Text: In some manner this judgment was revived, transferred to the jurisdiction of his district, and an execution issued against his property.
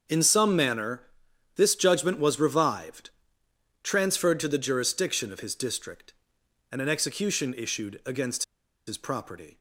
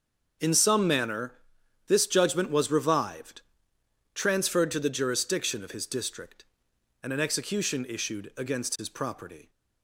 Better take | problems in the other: second | starts louder than the rest; strong; until 1.6 s; 7 dB; also in the second // pauses between "manner" and "this"; noticeable; at 1.0 s; 0.54 s long; noticeable in the second // pauses between "against" and "his"; at 8.4 s; 0.43 s long

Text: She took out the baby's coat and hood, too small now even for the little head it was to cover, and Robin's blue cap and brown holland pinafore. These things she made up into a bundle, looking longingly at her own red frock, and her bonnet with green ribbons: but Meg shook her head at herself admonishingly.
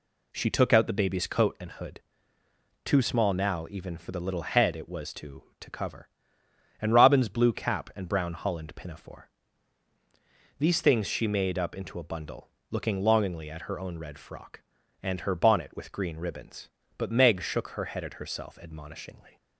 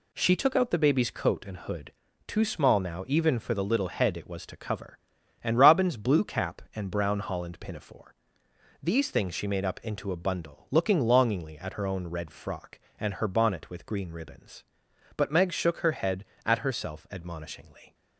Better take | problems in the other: second | says "to" twice; at 5.6 s

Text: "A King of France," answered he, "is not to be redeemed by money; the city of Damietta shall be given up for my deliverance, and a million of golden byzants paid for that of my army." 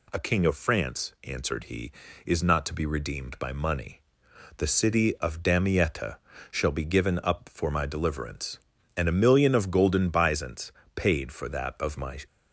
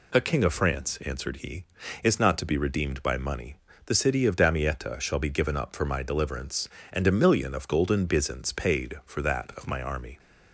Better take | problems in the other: second | pauses between "Damietta" and "shall"; slight; at 6.1 s; 0.32 s long // pauses between "byzants" and "paid"; slight; at 10.7 s; 0.24 s long // stops before "army"; at 12.2 s

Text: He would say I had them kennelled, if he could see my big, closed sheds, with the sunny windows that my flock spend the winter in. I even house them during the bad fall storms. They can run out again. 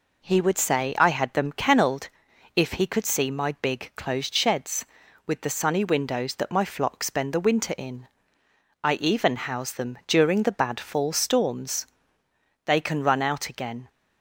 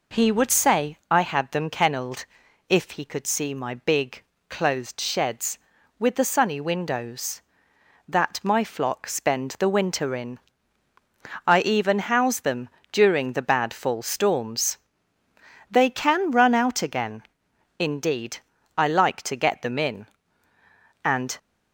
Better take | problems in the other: first | pauses between "them" and "during"; slight; at 12.6 s; 0.24 s long // goes on to say "Indeed I like to get them in and"; strong; from 17.7 s on; 3.6 s long

